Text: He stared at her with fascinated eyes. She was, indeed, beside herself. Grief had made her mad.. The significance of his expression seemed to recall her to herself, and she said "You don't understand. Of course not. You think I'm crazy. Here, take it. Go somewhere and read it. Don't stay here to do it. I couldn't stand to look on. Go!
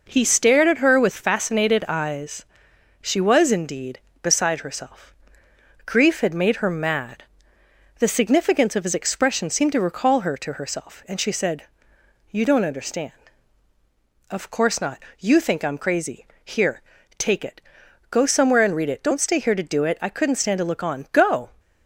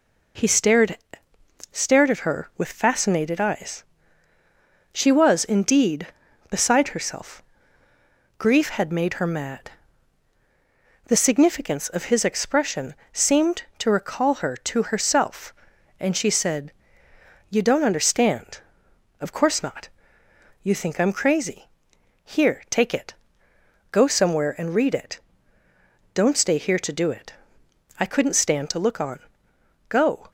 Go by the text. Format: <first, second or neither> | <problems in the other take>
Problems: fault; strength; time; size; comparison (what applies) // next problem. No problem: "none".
first | says "stared" twice; at 1.7 s // pauses between "expression" and "seemed"; slight; at 12.9 s; 0.22 s long // pauses between "said" and "You"; noticeable; at 16.7 s; 0.78 s long; noticeable in the first